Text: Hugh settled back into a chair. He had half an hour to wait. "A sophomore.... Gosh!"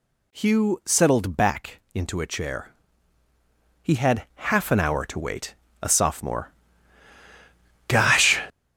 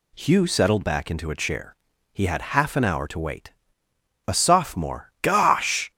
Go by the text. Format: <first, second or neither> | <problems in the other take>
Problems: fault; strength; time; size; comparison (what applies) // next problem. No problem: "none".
second | gets louder; strong; throughout; 10 dB